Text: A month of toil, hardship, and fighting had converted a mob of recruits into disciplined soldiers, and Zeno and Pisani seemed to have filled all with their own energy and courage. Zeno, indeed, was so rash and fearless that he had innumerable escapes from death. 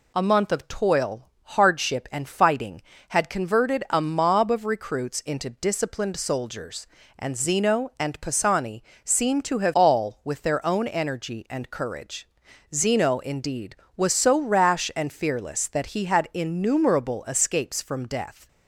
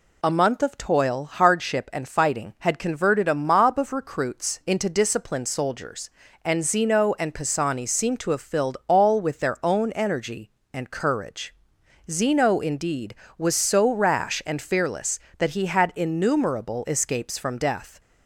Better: second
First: pauses between "Pisani" and "seemed"; slight; at 8.8 s; 0.22 s long // skips "filled"; at 9.7 s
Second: none

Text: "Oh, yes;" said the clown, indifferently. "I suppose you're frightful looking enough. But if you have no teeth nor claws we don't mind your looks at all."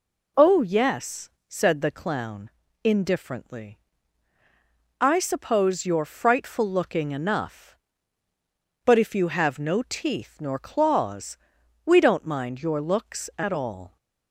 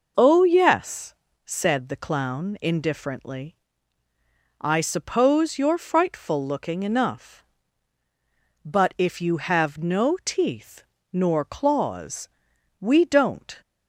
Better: first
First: pauses between "claws" and "we"; noticeable; at 11.3 s; 0.48 s long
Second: pauses between "teeth" and "nor"; slight; at 10.8 s; 0.26 s long // pauses between "claws" and "we"; noticeable; at 12.2 s; 0.50 s long // stops before "mind your looks at all"; at 13.6 s

